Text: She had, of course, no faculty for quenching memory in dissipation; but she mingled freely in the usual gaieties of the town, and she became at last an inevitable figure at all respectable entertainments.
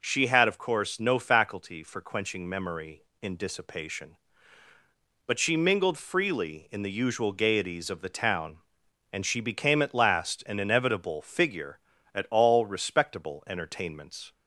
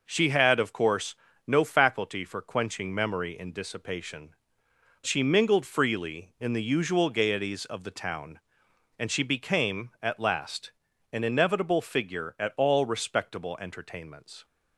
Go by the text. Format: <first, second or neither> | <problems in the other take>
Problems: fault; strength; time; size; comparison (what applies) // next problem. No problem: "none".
first | skips "but"; at 4.7 s // pauses between "last" and "an"; at 10.7 s; 0.42 s long